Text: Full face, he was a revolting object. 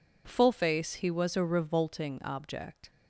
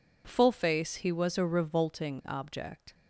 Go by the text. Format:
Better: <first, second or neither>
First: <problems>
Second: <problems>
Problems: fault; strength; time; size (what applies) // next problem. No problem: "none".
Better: neither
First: none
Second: none